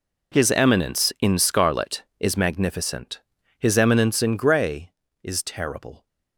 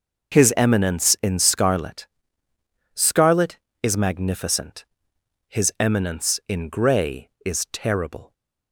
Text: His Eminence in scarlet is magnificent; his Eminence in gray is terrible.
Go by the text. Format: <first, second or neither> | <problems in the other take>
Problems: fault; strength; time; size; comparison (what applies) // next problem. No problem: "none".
first | starts louder than the rest; noticeable; until 1.4 s; 6 dB // says "scarlet" twice; at 2.9 s